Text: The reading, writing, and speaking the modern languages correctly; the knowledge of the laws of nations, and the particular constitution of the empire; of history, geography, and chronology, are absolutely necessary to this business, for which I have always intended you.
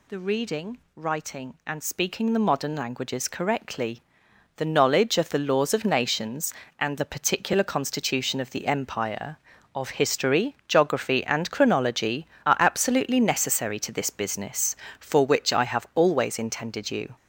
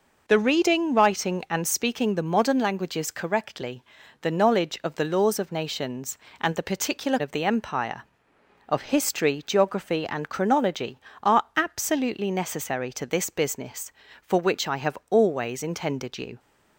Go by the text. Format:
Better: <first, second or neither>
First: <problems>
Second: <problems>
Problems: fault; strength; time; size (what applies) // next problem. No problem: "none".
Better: first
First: none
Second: skips "constitution"; at 7.1 s